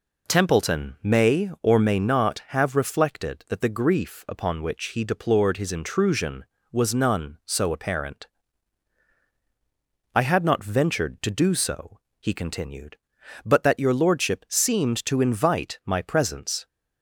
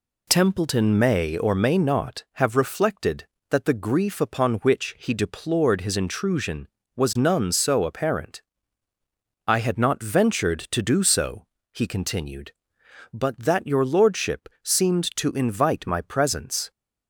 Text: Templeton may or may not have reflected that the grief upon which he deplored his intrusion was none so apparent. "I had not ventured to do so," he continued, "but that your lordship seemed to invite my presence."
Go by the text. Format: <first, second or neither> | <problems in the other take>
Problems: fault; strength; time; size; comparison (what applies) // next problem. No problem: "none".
neither | none